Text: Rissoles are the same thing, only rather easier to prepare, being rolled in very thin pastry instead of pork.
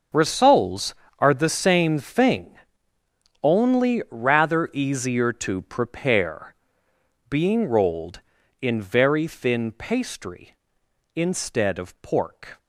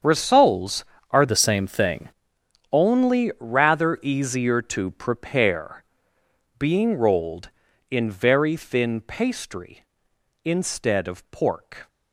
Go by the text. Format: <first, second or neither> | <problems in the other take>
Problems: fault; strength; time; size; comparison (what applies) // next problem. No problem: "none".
first | starts louder than the rest; strong; until 1.3 s; 7.5 dB; also in the first // changes voice from "the" to "thing"; from 1.2 to 2.0 s; 0.8 s long